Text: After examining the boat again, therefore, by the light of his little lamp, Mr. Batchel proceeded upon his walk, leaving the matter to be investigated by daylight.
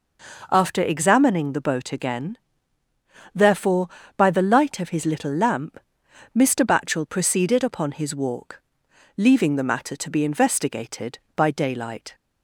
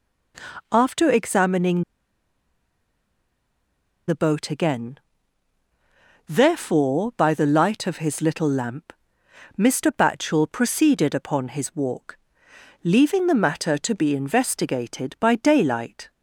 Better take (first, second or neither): first